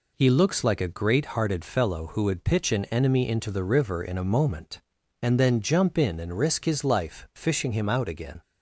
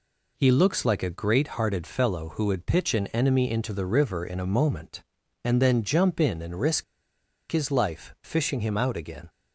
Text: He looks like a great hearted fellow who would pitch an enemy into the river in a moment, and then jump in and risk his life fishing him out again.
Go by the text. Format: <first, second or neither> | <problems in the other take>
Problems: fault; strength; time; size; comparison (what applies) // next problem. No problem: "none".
first | pauses between "risk" and "his"; noticeable; at 6.8 s; 0.67 s long